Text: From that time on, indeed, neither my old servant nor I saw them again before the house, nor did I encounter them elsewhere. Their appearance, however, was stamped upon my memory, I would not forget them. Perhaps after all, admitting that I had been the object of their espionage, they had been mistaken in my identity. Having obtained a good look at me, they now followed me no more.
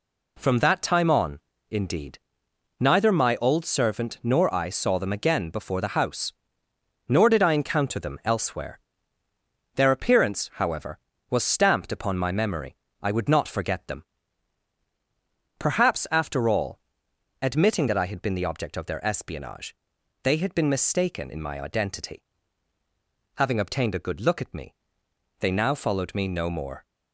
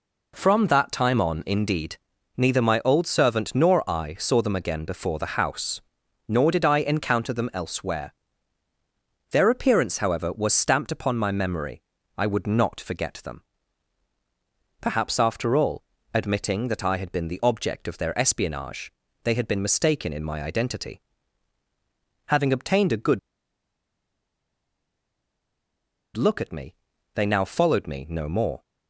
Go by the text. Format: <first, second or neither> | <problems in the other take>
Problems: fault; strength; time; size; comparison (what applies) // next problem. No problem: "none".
first | pauses between "good" and "look"; strong; at 23.1 s; 2.9 s long